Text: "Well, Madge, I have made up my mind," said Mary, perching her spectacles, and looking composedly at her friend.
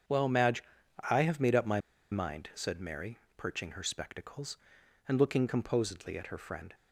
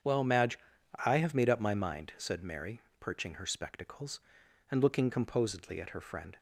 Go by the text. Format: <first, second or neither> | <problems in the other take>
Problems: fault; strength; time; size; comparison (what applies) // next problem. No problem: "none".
second | starts louder than the rest; until 1.4 s; 7 dB; strong in the second // pauses between "my" and "mind"; slight; at 1.7 s; 0.31 s long